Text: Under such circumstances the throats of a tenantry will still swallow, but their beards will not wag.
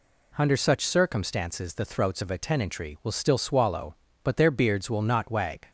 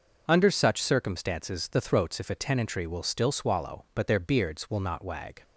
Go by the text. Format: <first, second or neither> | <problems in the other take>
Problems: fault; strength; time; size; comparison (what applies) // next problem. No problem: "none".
first | starts louder than the rest; noticeable; until 1.2 s; 6 dB // says "if" for "of"; at 2.2 s